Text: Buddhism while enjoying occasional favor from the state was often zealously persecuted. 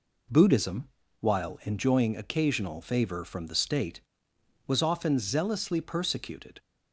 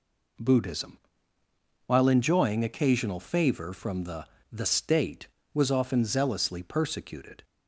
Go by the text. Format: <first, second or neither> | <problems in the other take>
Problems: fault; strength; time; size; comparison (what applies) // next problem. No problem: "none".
first | pauses between "Buddhism" and "while"; noticeable; at 0.9 s; 0.88 s long; slight in the first // says "the" twice; at 4.5 s